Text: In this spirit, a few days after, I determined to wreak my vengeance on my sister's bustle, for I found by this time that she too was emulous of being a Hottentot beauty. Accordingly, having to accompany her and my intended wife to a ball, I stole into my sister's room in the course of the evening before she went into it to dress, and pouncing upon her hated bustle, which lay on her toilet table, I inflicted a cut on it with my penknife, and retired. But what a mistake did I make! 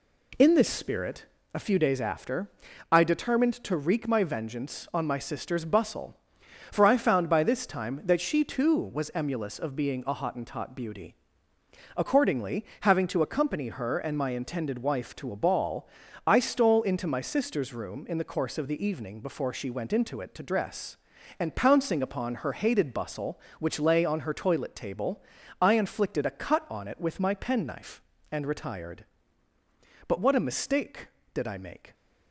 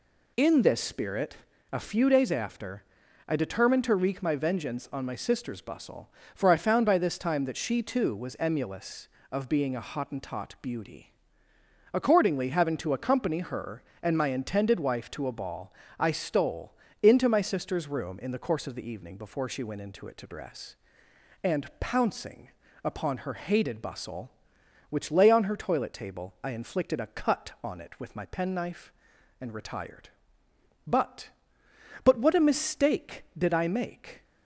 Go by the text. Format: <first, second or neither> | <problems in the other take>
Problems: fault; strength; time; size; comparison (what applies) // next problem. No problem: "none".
first | pauses between "stole" and "into"; slight; at 16.7 s; 0.26 s long // pauses between "pouncing" and "upon"; slight; at 22.4 s; 0.34 s long // says "But" twice; at 32.0 s